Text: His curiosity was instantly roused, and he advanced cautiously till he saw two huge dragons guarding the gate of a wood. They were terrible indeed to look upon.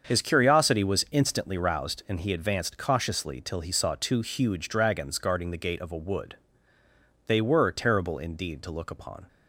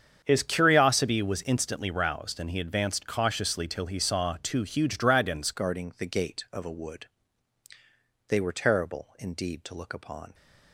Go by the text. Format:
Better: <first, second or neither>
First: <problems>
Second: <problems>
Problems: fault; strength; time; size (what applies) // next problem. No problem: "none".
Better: first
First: starts louder than the rest; until 1.1 s; 7 dB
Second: starts louder than the rest; strong; until 1.2 s; 7.5 dB // changes voice at "guarding"; from 5.5 s on; 4.8 s long